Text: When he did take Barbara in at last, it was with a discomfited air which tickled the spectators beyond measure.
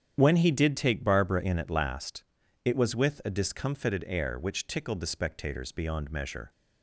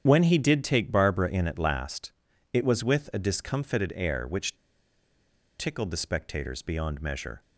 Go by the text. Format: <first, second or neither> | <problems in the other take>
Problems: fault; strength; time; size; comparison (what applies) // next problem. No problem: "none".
first | starts louder than the rest; strong; until 1.0 s; 9 dB; strong in the first // pauses between "which" and "tickled"; at 4.5 s; 1.0 s long